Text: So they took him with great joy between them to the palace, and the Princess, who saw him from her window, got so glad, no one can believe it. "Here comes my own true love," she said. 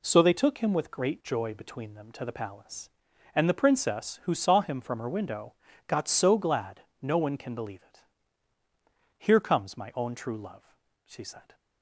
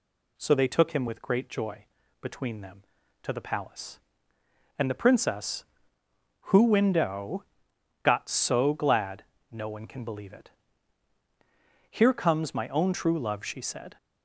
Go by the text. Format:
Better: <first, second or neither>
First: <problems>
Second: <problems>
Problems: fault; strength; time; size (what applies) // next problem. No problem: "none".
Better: first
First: none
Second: pauses between "joy" and "between"; slight; at 1.8 s; 0.36 s long // skips "saw him from her"; at 6.6 s